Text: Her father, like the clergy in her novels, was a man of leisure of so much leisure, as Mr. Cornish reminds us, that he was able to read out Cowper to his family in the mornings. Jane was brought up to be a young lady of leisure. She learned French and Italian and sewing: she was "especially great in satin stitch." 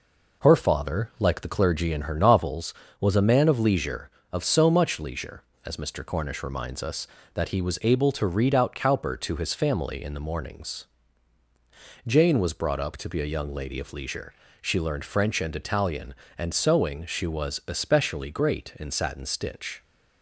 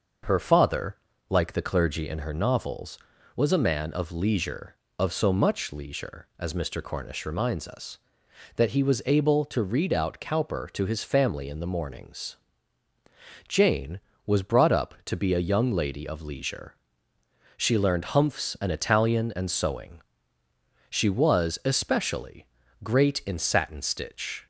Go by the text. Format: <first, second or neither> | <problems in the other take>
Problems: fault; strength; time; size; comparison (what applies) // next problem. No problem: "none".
first | starts louder than the rest; noticeable; until 1.5 s; 6 dB // says "Humphs" for "French"; at 18.0 s // pauses between "especially" and "great"; slight; at 22.4 s; 0.36 s long